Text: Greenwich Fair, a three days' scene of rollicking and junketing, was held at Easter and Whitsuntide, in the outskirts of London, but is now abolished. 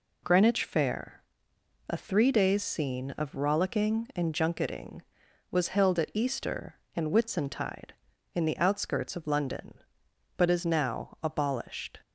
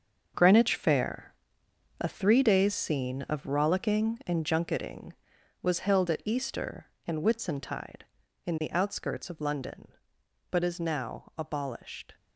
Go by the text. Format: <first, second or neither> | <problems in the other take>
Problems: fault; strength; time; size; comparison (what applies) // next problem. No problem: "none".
first | gets quieter; strong; throughout; 10 dB